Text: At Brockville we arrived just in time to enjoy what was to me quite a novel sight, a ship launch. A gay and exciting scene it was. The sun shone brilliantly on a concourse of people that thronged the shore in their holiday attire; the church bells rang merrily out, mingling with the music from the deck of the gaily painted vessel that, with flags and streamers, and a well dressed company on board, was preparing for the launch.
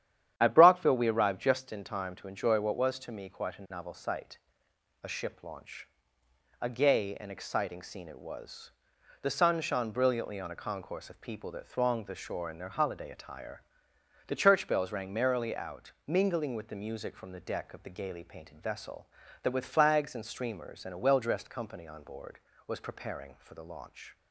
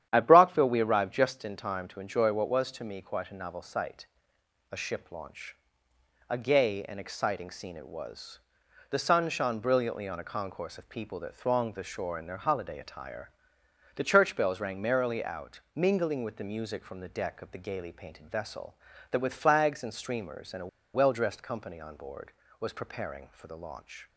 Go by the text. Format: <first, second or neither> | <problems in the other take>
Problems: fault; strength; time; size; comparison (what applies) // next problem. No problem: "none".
first | starts louder than the rest; strong; until 1.1 s; 10 dB; strong in the first // pauses between "a" and "well"; slight; at 20.6 s; 0.27 s long